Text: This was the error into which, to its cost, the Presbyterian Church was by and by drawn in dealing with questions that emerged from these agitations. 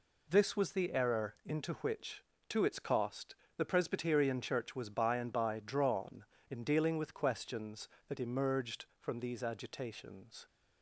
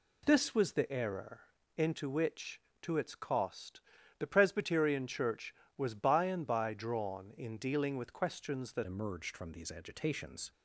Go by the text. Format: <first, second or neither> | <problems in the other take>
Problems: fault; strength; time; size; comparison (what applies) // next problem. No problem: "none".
first | pauses between "error" and "into"; slight; at 1.4 s; 0.34 s long // changes voice at "emerged"; from 8.8 s on; 1.7 s long